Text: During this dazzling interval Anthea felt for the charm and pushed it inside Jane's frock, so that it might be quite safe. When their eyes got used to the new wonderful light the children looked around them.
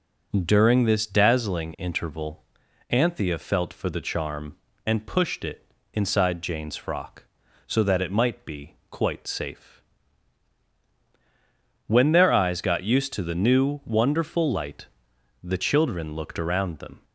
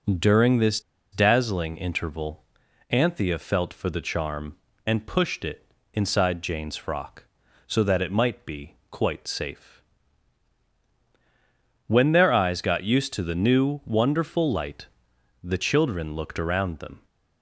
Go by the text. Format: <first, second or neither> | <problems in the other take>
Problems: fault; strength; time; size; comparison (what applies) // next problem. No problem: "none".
first | pauses between "this" and "dazzling"; slight; at 0.8 s; 0.31 s long // pauses between "interval" and "Anthea"; noticeable; at 2.4 s; 0.48 s long; noticeable in the first // pauses between "it" and "inside"; slight; at 5.6 s; 0.28 s long; slight in the first // pauses between "be" and "quite"; slight; at 8.7 s; 0.16 s long; slight in the first // pauses between "light" and "the"; noticeable; at 14.8 s; 0.56 s long; noticeable in the first